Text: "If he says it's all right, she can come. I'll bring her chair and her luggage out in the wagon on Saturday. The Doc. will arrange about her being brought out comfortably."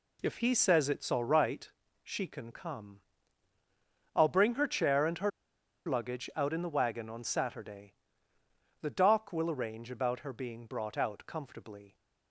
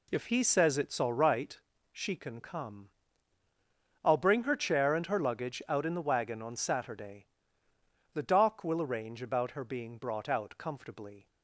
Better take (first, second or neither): second